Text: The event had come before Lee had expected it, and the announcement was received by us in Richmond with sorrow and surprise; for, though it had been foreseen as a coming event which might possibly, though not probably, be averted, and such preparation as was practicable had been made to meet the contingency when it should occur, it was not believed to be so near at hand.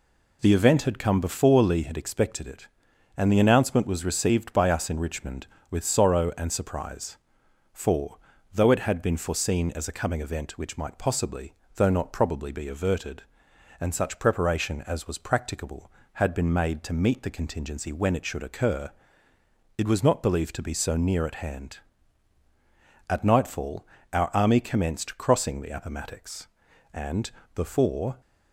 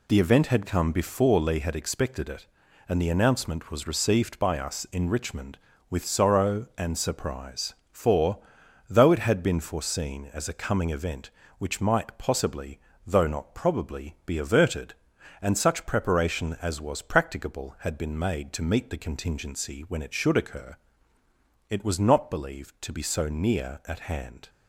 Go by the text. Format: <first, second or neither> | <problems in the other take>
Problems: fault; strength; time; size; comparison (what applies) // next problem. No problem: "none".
second | goes on to say "At nightfall our army commenced crossing the Appomattox and before"; strong; from 23.1 s on; 5.1 s long